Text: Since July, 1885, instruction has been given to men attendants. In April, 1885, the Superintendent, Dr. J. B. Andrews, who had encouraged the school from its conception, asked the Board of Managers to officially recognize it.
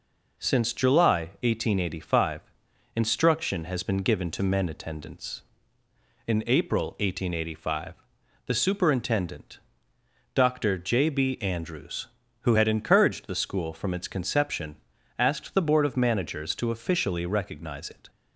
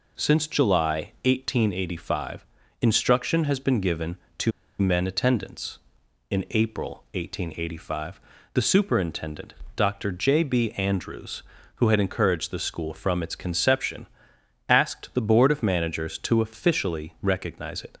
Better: first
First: none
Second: pauses between "to" and "men"; slight; at 4.5 s; 0.28 s long

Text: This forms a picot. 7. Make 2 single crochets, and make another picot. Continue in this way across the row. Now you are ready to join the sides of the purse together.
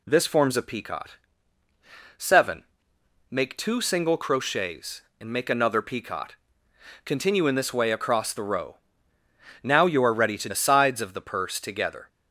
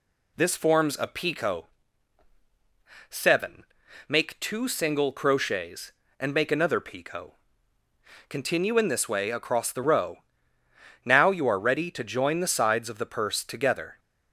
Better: second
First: skips "join"; at 10.4 s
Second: none

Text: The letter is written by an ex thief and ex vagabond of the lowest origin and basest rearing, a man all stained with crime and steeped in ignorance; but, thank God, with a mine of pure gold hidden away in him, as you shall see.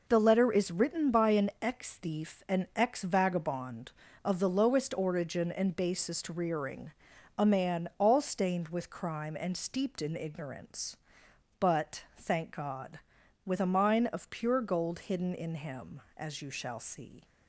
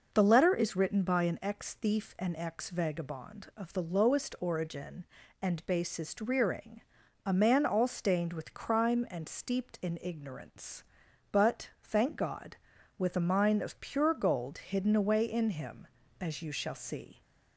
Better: second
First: skips "away"; at 15.3 s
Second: none

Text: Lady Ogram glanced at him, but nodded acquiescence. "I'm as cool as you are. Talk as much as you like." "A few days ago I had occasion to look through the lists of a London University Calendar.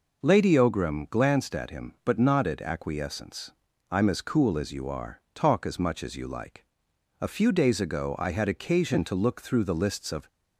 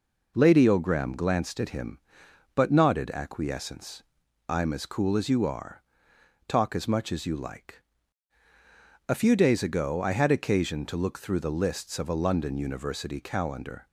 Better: second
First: stops before "a London University Calendar"; at 10.2 s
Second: none

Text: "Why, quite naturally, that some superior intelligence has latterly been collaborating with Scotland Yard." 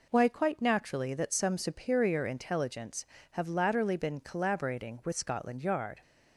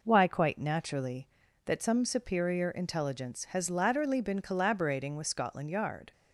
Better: second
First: says "have" for "has"; at 3.3 s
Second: none

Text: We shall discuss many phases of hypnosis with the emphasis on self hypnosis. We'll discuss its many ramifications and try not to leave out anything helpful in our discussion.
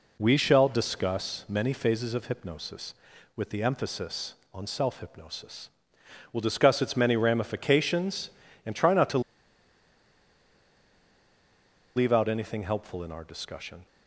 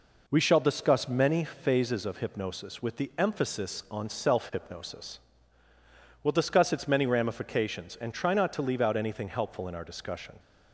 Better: second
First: pauses between "to" and "leave"; strong; at 9.1 s; 2.7 s long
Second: none

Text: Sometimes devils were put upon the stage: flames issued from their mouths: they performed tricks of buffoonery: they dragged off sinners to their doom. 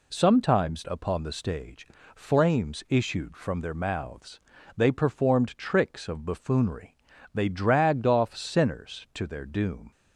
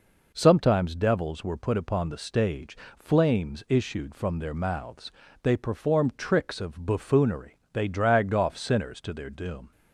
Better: second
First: skips "devils were put"; at 0.8 s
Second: none

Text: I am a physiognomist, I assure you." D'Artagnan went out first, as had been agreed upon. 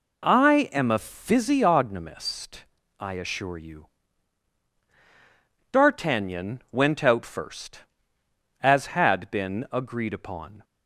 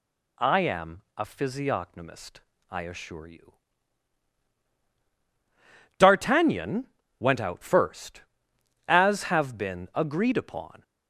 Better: first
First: none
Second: pauses between "D'Artagnan" and "went"; slight; at 6.8 s; 0.32 s long // says "have" for "had"; at 9.2 s

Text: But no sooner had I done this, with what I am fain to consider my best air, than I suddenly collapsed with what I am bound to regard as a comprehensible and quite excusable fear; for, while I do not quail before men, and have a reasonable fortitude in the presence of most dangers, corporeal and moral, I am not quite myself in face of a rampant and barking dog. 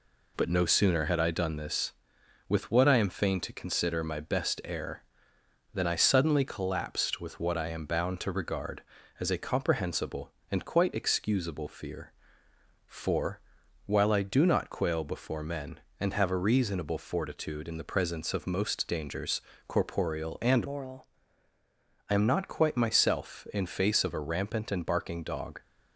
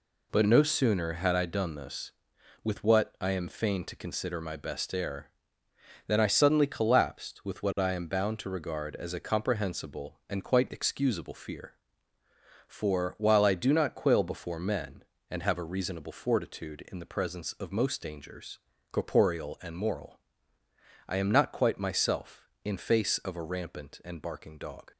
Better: second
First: changes voice from "moral" to "I"; from 20.6 to 21.0 s; 0.4 s long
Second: none

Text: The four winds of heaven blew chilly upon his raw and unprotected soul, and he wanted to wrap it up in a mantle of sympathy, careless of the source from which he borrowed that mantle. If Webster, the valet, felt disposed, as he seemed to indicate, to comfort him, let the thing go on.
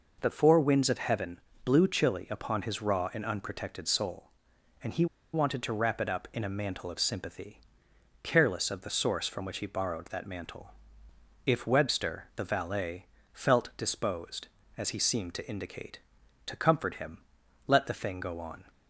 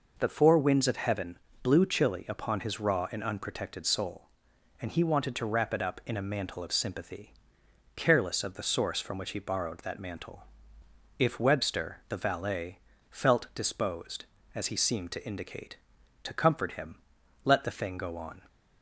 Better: second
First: pauses between "heaven" and "blew"; slight; at 1.3 s; 0.24 s long // pauses between "he" and "wanted"; slight; at 5.0 s; 0.28 s long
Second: pauses between "heaven" and "blew"; slight; at 1.3 s; 0.24 s long

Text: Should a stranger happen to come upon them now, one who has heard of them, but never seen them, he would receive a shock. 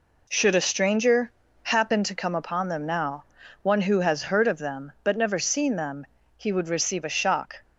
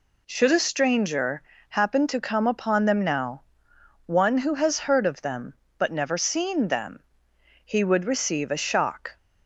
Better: neither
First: pauses between "stranger" and "happen"; slight; at 1.3 s; 0.32 s long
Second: pauses between "stranger" and "happen"; slight; at 1.4 s; 0.26 s long

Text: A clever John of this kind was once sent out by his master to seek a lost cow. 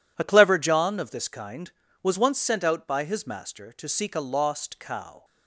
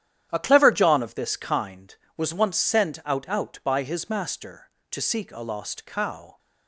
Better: first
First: none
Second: starts louder than the rest; strong; until 1.3 s; 11 dB // says "out" twice; at 3.3 s

